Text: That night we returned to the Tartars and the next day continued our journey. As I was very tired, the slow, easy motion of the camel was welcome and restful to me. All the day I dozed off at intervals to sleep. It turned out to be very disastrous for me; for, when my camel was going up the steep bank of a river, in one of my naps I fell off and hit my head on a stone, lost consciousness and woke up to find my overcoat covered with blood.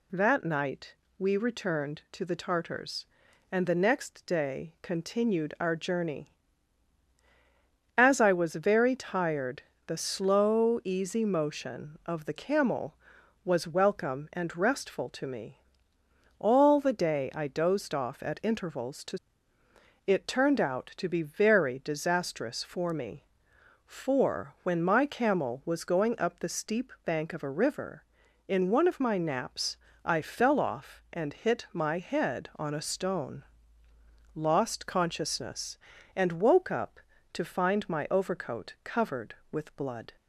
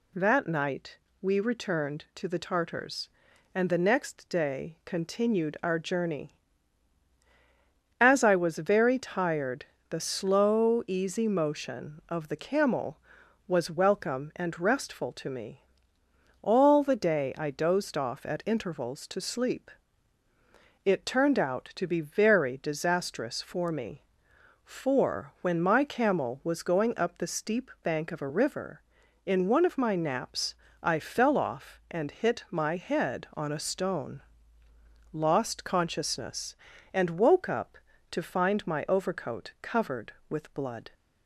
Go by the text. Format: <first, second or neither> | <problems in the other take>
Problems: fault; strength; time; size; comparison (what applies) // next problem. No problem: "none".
second | pauses between "night" and "we"; slight; at 0.9 s; 0.24 s long; slight in the second // skips "sleep"; at 19.6 s // pauses between "naps" and "I"; slight; at 29.7 s; 0.28 s long; slight in the second